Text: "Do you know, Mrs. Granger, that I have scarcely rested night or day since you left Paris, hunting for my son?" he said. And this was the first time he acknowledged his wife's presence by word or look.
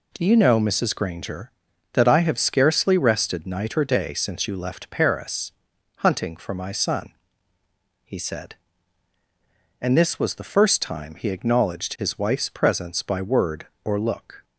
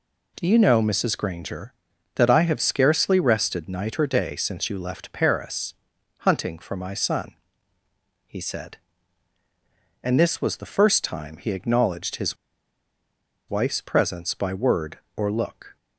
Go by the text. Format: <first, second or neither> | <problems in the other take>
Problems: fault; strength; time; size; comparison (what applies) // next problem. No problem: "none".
first | pauses between "his" and "wife's"; at 12.3 s; 1.1 s long